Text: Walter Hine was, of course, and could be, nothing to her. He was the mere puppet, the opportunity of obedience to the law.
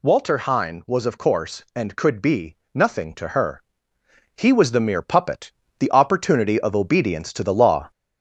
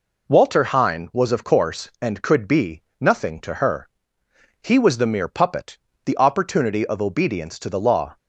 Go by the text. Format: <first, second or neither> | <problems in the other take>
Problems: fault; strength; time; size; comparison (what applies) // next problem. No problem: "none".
second | gets louder; slight; throughout; 2 dB